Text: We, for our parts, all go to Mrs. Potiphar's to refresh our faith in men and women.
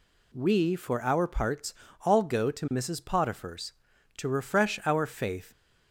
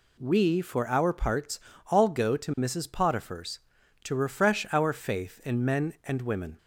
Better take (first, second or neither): second